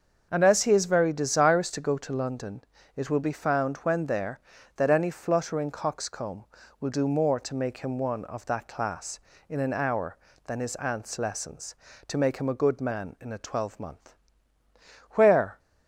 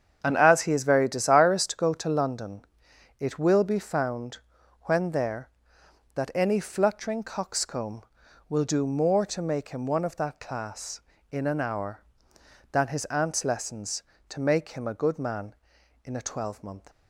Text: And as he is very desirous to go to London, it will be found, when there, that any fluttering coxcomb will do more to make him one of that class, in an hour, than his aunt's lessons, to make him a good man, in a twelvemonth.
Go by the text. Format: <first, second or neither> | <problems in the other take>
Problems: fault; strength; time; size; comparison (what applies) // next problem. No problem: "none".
second | starts louder than the rest; until 1.3 s; 6.5 dB; strong in the second // goes on to say "Where"; slight; from 15.1 s on; 0.48 s long